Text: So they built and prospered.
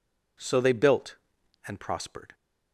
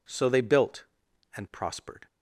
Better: neither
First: none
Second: none

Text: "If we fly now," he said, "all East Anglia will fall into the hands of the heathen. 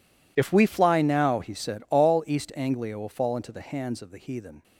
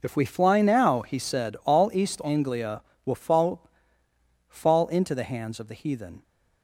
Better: first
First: none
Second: says "fall" twice; at 4.4 s

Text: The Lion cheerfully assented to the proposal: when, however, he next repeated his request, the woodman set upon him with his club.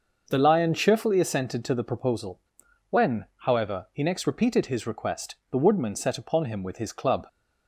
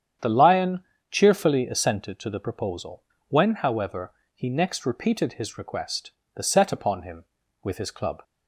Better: first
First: starts louder than the rest; noticeable; until 1.3 s; 6 dB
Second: starts louder than the rest; strong; until 1.4 s; 8.5 dB // pauses between "Lion" and "cheerfully"; slight; at 0.8 s; 0.28 s long // skips "woodman"; at 6.4 s

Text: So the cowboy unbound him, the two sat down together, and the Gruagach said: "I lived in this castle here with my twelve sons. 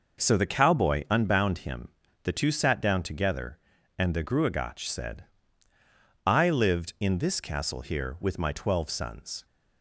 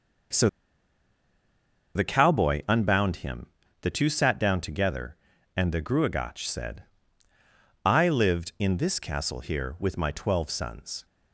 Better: first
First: none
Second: pauses between "So" and "the"; strong; at 0.4 s; 1.4 s long

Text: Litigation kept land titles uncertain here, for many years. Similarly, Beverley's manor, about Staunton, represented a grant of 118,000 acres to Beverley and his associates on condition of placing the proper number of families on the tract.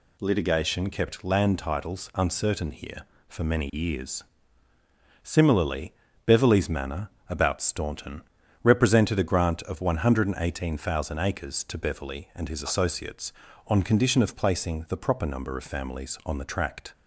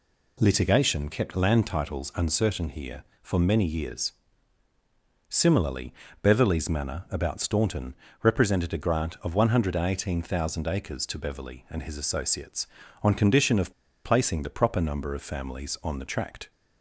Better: first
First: none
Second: pauses between "of" and "placing"; slight; at 13.7 s; 0.32 s long

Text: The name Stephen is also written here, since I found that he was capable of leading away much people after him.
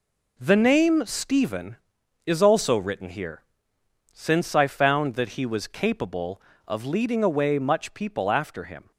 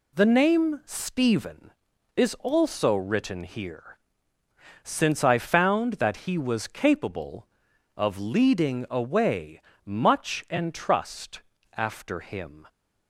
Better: first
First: none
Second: pauses between "away" and "much"; slight; at 9.5 s; 0.28 s long // says "entrust" for "people"; at 10.5 s

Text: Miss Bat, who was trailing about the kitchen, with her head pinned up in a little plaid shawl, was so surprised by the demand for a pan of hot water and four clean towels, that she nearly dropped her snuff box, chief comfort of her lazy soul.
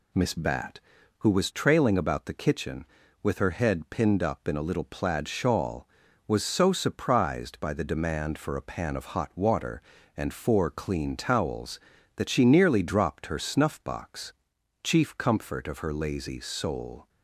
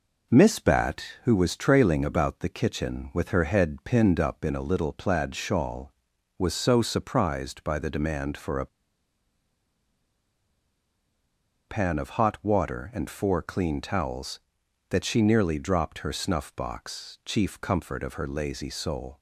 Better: first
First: none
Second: pauses between "a" and "pan"; strong; at 8.6 s; 3.0 s long

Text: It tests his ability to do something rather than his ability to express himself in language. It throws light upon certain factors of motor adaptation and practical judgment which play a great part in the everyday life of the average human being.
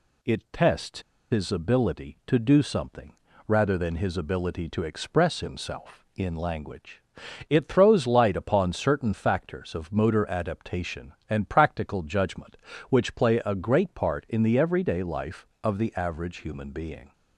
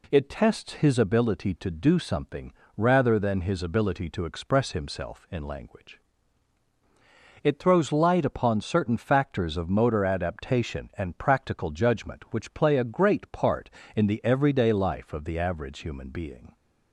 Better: second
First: pauses between "tests" and "his"; slight; at 0.9 s; 0.31 s long // pauses between "something" and "rather"; slight; at 3.1 s; 0.32 s long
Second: pauses between "something" and "rather"; slight; at 2.5 s; 0.24 s long

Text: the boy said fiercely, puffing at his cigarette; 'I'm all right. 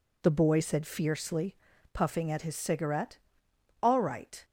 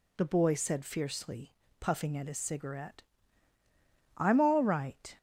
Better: second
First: skips "I'm"; at 3.4 s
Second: none

